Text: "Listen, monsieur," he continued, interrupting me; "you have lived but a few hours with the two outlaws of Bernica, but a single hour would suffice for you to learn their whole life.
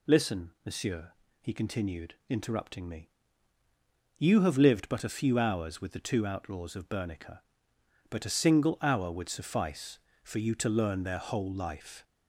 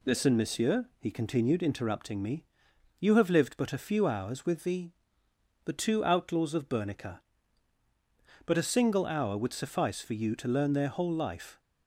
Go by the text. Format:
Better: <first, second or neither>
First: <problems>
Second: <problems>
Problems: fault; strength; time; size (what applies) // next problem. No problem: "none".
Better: first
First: none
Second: says "the" twice; at 5.6 s